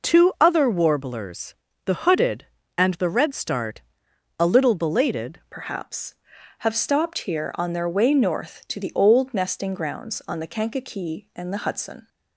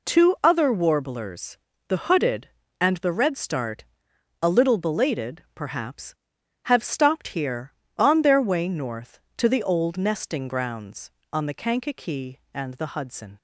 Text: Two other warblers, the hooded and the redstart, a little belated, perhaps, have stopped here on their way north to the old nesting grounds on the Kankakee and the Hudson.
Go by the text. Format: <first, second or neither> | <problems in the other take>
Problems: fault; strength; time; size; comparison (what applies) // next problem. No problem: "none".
second | changes voice at "perhaps"; from 5.5 s on; 6.5 s long